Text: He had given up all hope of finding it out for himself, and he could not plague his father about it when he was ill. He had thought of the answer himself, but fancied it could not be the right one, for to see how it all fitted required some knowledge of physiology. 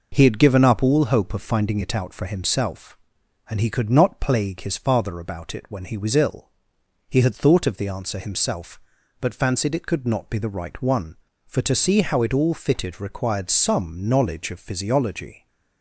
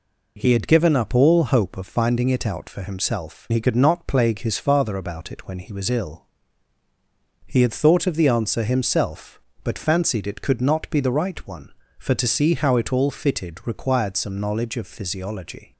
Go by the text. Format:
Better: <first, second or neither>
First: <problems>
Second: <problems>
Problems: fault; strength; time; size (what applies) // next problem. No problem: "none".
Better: first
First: none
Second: skips "and"; at 3.4 s